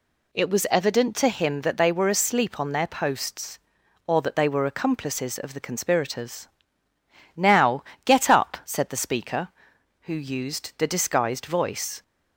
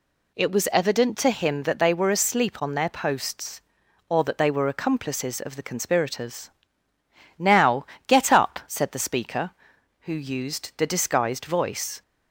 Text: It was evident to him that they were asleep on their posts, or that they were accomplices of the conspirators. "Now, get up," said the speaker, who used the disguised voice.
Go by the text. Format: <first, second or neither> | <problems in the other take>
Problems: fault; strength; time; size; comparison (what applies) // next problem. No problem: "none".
neither | none